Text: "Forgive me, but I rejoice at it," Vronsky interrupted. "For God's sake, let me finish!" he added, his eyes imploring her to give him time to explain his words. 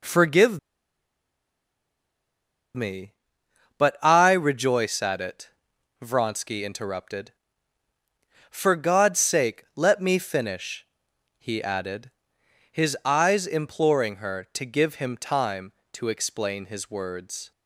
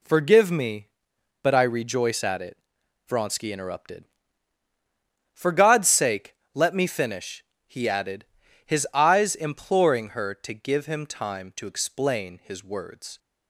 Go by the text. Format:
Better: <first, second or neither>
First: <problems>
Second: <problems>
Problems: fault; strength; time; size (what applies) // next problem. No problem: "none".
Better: second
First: pauses between "Forgive" and "me"; strong; at 0.5 s; 2.1 s long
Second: none